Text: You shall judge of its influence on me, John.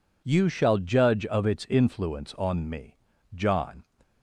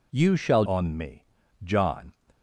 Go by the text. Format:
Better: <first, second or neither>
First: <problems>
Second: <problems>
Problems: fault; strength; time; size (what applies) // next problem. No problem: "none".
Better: first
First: none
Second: skips "judge of its influence"; at 0.6 s